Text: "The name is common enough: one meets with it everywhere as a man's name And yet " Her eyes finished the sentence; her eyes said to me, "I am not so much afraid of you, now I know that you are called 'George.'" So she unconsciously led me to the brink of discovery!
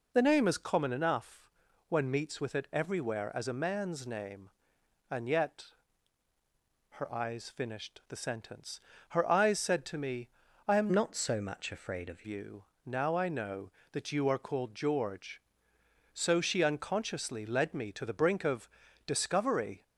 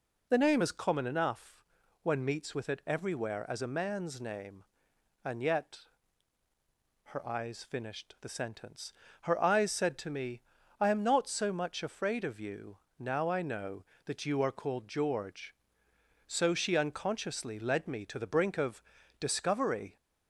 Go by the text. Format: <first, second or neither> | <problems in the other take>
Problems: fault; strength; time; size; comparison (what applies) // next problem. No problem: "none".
second | changes voice from "not" to "of"; from 10.9 to 12.2 s; 1.3 s long // pauses between "of" and "discovery"; at 18.6 s; 0.38 s long; also in the second